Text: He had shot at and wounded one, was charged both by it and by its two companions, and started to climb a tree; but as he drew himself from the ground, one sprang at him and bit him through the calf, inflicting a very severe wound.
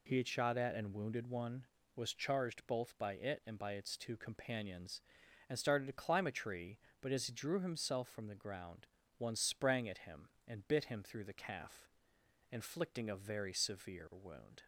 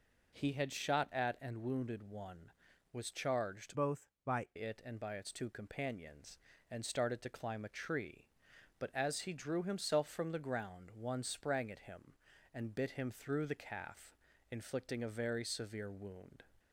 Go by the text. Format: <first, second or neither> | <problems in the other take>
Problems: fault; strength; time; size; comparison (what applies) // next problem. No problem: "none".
first | changes voice from "both" to "by"; from 3.7 to 4.4 s; 0.7 s long